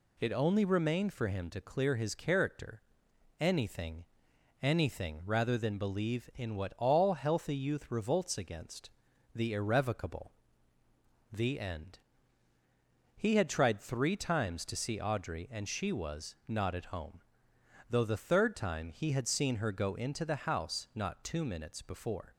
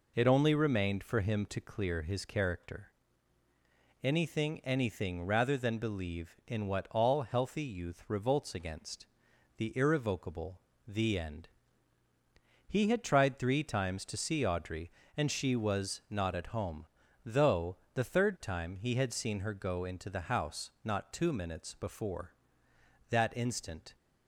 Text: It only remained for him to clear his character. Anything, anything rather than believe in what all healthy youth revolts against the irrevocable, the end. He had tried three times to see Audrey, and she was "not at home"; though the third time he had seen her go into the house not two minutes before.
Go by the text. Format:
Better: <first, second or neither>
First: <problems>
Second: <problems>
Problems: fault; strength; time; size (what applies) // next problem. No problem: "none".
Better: first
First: pauses between "against" and "the"; at 8.9 s; 0.44 s long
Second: pauses between "against" and "the"; noticeable; at 9.0 s; 0.52 s long // pauses between "though" and "the"; slight; at 17.7 s; 0.16 s long // goes on to say "That instant"; noticeable; from 23.1 s on; 0.86 s long